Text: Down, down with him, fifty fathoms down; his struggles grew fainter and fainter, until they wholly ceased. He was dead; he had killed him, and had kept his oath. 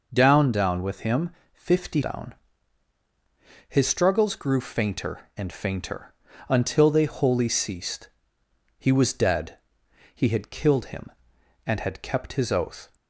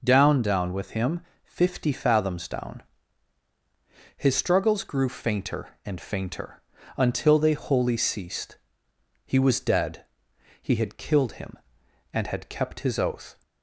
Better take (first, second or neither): second